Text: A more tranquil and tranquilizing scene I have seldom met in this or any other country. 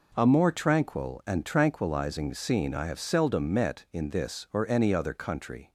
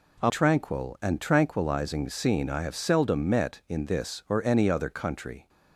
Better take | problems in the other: first | skips "more"; at 0.2 s

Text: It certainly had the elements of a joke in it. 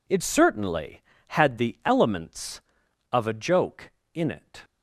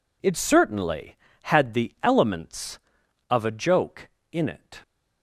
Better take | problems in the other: neither | none

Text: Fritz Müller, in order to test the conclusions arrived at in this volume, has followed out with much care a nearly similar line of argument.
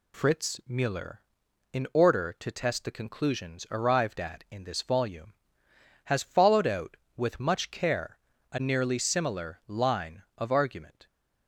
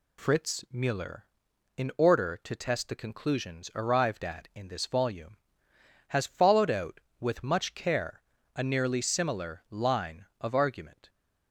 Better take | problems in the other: neither | pauses between "care" and "a"; slight; the same in both

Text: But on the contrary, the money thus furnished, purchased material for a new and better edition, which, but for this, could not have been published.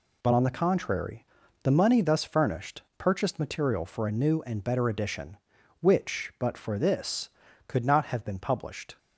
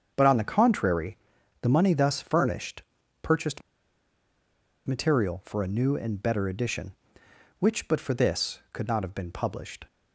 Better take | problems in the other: first | starts louder than the rest; strong; until 1.1 s; 7.5 dB // pauses between "purchased" and "material"; strong; at 3.6 s; 1.2 s long

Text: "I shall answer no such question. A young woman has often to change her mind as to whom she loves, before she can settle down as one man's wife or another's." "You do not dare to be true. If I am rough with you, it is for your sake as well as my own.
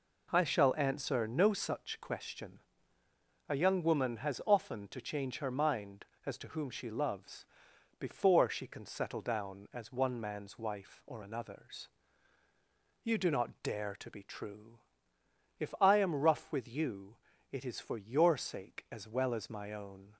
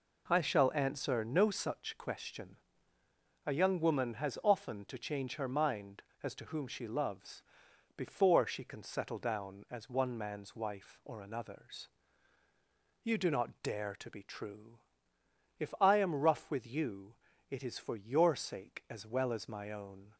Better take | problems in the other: neither | none

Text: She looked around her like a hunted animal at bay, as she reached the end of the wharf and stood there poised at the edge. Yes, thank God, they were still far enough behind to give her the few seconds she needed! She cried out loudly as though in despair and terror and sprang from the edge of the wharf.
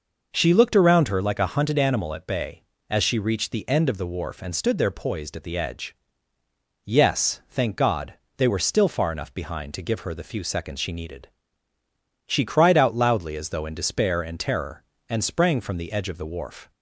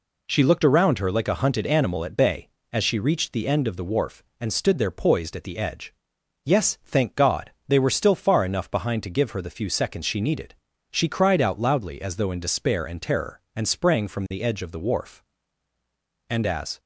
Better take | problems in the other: first | goes on to say "And as"; from 16.2 s on; 0.50 s long

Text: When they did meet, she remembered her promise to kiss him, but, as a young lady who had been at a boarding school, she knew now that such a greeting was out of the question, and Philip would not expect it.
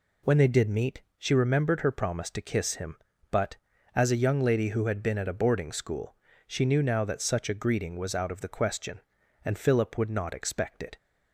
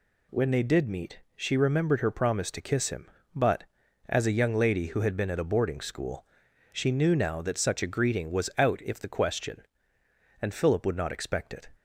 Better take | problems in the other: first | says "if" for "of"; at 8.8 s

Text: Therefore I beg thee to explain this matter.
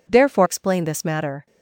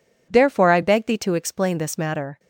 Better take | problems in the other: second | skips "I beg thee to"; at 0.4 s

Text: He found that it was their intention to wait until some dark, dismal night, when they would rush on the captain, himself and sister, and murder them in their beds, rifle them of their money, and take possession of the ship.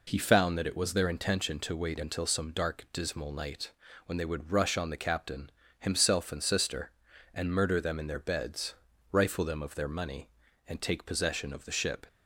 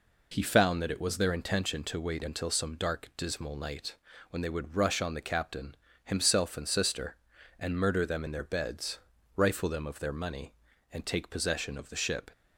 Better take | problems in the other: neither | none

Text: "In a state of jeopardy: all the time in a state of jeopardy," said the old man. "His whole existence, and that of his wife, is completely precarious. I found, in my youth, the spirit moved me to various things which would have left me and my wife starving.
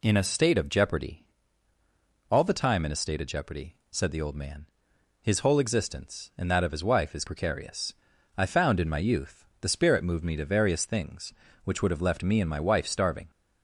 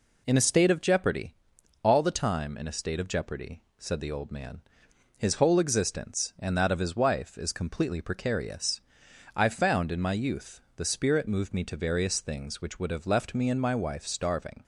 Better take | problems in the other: second | skips "completely"; at 7.2 s

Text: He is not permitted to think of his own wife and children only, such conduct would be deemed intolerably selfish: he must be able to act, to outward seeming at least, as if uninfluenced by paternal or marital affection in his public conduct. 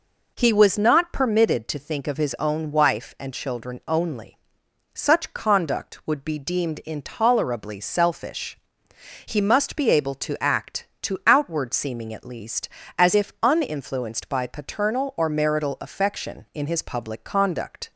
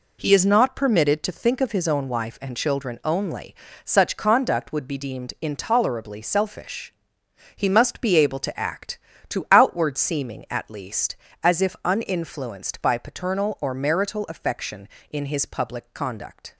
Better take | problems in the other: second | says "was" for "is"; at 0.5 s

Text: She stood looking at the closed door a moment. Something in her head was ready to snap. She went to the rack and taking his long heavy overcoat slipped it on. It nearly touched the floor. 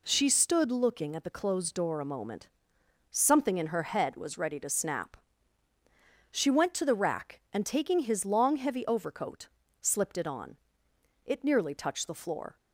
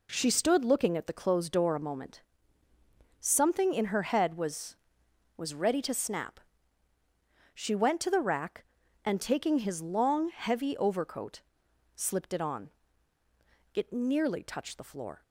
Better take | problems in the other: first | says "was" twice; at 5.3 s // pauses between "overcoat" and "slipped"; noticeable; at 11.4 s; 0.54 s long; slight in the first

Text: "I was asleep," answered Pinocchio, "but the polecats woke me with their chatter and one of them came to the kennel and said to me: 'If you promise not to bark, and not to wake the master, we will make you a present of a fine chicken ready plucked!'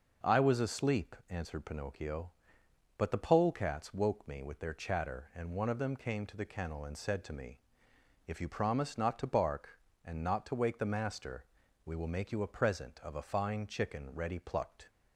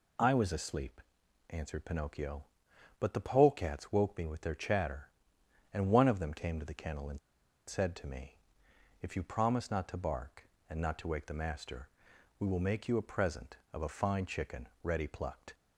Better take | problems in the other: first | pauses between "and" and "said"; noticeable; at 7.1 s; 0.48 s long // pauses between "chicken" and "ready"; slight; at 14.6 s; 0.16 s long

